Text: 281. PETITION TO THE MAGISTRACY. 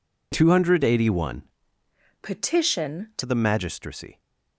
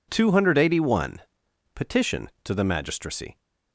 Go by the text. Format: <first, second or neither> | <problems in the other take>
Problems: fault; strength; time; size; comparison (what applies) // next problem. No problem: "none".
second | changes voice from "PETITION" to "TO"; from 2.2 to 3.2 s; 1.0 s long